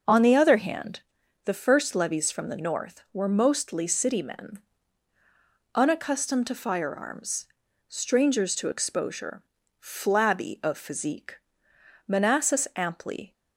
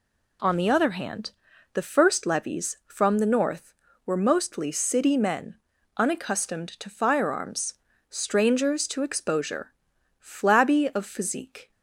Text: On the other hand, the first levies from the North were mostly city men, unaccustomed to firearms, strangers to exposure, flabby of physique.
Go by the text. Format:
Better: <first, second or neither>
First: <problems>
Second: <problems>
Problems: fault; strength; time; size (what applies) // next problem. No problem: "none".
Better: second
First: starts louder than the rest; until 1.5 s; 6 dB // goes on to say "Manassas amply"; noticeable; from 12.0 s on; 1.2 s long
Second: none